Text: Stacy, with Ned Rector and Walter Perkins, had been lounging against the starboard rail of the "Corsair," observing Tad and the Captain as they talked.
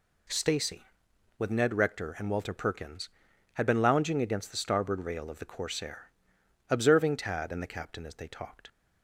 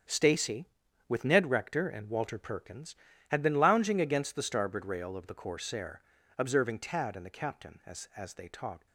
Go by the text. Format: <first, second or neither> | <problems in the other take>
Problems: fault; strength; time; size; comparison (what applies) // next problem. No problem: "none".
first | starts louder than the rest; strong; until 1.5 s; 7.5 dB // says "as" twice; at 8.1 s